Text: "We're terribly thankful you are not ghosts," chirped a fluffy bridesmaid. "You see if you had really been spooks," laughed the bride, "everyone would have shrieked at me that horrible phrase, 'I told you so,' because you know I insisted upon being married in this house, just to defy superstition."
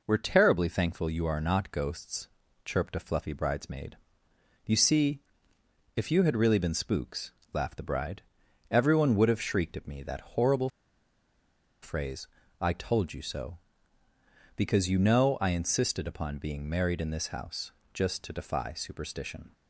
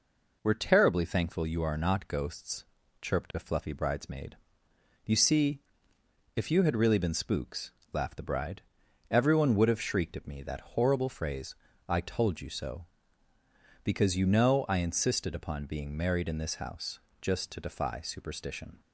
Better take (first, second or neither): second